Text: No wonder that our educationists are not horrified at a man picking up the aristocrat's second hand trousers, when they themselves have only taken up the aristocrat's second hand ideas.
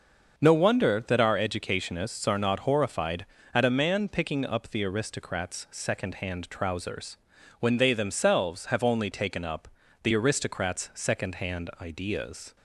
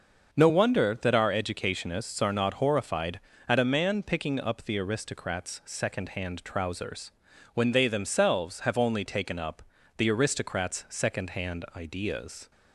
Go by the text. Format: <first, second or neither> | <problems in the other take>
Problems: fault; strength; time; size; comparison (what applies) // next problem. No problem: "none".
neither | starts louder than the rest; the same in both // pauses between "up" and "the"; slight; the same in both